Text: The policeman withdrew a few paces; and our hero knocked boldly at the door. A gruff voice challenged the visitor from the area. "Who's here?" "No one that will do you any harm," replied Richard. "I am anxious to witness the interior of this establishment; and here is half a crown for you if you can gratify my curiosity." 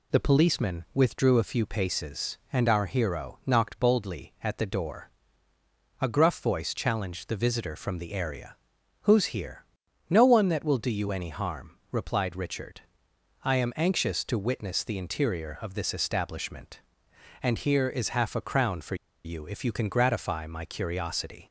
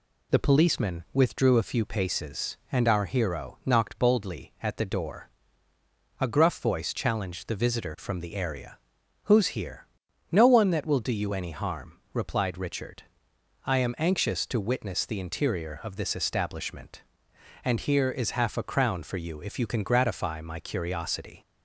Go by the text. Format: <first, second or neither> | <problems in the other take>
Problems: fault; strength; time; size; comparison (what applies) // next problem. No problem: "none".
second | pauses between "for" and "you"; slight; at 18.9 s; 0.29 s long